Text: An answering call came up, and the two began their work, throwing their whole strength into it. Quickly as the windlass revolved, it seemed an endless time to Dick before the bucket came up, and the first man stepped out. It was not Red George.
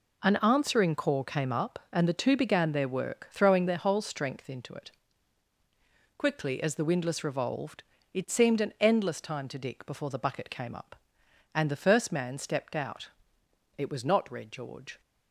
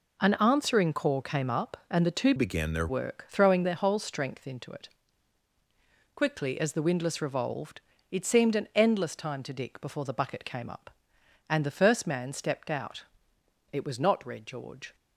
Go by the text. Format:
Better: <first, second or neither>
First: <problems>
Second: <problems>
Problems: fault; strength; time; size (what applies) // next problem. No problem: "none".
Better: first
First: none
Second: changes voice from "began" to "their"; from 2.3 to 2.8 s; 0.5 s long